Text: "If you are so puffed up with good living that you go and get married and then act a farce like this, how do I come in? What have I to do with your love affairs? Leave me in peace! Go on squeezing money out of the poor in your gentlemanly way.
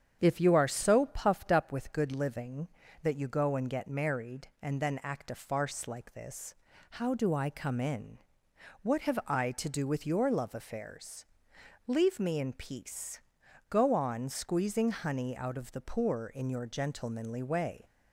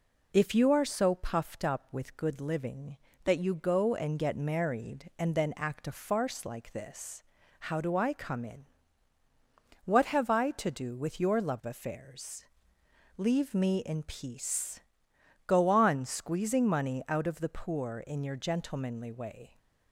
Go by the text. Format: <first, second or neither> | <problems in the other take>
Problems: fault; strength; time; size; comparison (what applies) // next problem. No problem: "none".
second | starts louder than the rest; strong; until 1.2 s; 8 dB // says "honey" for "money"; at 14.8 s